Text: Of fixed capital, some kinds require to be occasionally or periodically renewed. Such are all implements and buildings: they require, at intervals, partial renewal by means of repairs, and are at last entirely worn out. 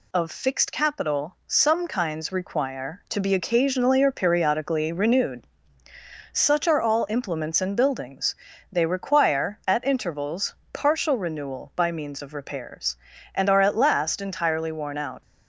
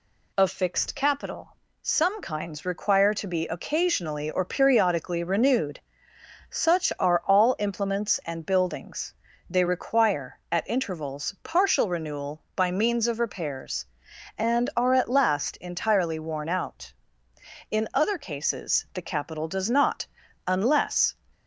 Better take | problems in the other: first | goes on to say "In other cases the capital does not unless"; strong; from 17.7 s on; 3.4 s long

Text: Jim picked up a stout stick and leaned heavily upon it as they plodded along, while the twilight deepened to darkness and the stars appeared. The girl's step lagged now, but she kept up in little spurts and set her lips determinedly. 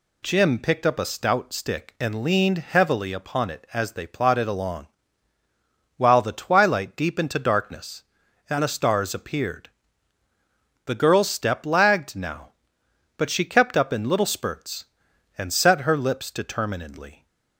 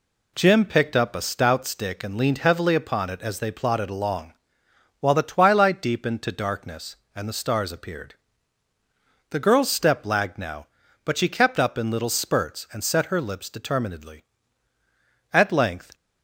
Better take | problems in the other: first | goes on to say "At length"; noticeable; from 15.3 s on; 0.62 s long

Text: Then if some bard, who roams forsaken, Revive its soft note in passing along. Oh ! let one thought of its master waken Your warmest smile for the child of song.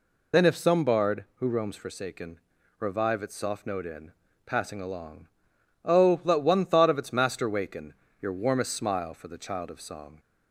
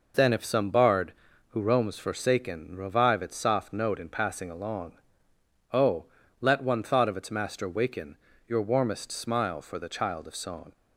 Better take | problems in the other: second | loses the start of "Then"; at 0.3 s; 40 ms // pauses between "in" and "passing"; slight; at 4.1 s; 0.34 s long // pauses between "waken" and "Your"; slight; at 7.9 s; 0.26 s long; slight in the second

